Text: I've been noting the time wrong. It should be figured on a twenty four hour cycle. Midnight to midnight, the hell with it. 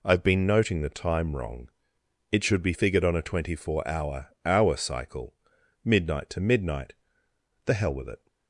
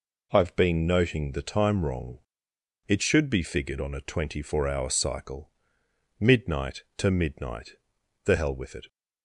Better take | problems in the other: second | says "hour" twice; at 4.4 s

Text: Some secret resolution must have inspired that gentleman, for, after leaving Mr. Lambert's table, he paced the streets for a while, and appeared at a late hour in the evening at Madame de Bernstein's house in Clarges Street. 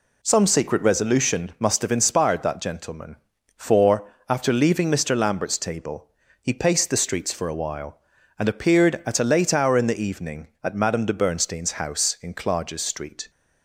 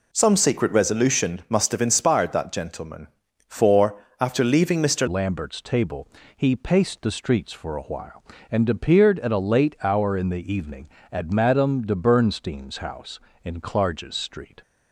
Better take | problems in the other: first | changes voice at "Lambert's"; from 5.0 s on; 9.6 s long

